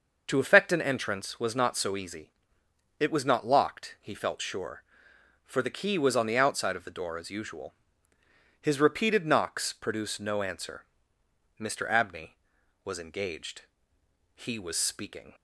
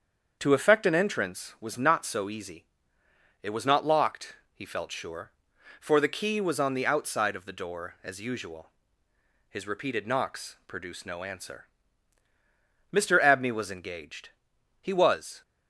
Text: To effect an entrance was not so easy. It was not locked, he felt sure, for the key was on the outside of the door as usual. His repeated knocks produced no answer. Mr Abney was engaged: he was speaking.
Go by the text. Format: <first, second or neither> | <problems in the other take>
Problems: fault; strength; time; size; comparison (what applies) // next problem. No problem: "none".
first | starts louder than the rest; until 1.4 s; 7 dB // stops before "speaking"; at 15.4 s